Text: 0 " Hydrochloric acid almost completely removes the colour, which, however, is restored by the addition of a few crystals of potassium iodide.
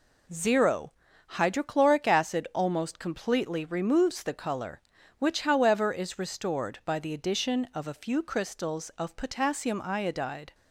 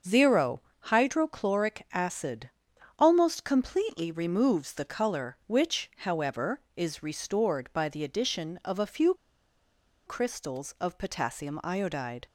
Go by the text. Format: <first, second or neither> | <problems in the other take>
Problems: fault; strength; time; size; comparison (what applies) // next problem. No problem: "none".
first | starts louder than the rest; until 1.2 s; 6.5 dB // pauses between "acid" and "almost"; noticeable; at 2.4 s; 0.50 s long // pauses between "few" and "crystals"; noticeable; at 9.1 s; 0.92 s long